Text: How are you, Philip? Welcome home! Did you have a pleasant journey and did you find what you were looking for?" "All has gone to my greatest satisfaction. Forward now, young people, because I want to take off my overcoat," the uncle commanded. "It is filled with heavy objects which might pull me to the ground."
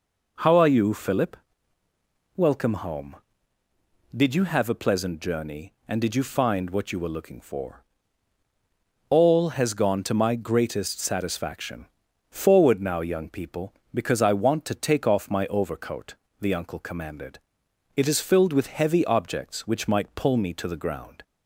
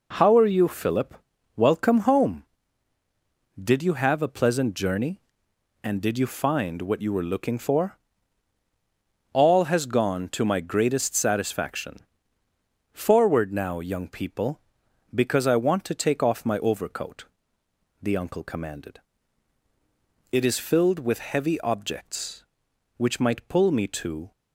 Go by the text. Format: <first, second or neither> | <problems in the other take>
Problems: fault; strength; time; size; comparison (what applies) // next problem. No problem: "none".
first | stops before "the ground"; at 24.3 s